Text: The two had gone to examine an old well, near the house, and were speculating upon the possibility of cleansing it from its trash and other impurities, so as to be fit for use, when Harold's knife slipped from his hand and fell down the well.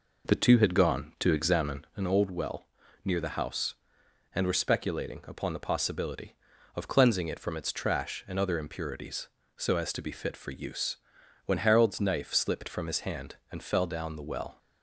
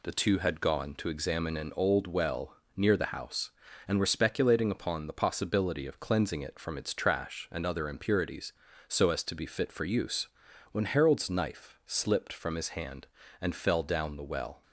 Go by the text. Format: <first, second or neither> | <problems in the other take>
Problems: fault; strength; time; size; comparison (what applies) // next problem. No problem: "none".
second | starts louder than the rest; noticeable; until 2.2 s; 4.5 dB